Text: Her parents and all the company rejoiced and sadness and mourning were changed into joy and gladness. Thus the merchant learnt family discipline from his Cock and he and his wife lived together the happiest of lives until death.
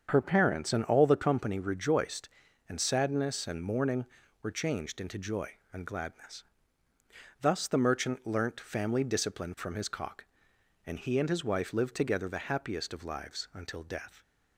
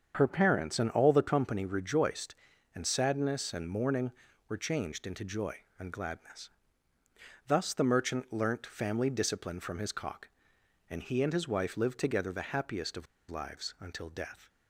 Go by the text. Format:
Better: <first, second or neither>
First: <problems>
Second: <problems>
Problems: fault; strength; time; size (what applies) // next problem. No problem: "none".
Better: first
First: starts louder than the rest; strong; until 1.1 s; 7 dB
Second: starts louder than the rest; strong; until 1.1 s; 7 dB // pauses between "of" and "lives"; slight; at 13.0 s; 0.24 s long